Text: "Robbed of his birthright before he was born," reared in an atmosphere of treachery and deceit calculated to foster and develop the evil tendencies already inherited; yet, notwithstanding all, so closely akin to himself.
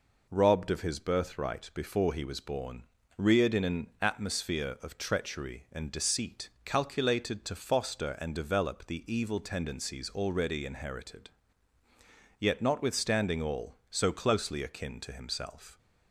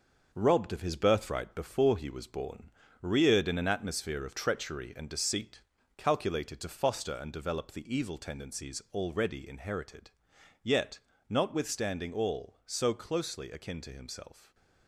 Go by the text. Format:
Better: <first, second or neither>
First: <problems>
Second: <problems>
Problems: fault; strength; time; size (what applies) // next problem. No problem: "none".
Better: first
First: pauses between "deceit" and "calculated"; slight; at 6.4 s; 0.16 s long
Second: gets quieter; throughout; 6.5 dB // pauses between "deceit" and "calculated"; slight; at 5.6 s; 0.36 s long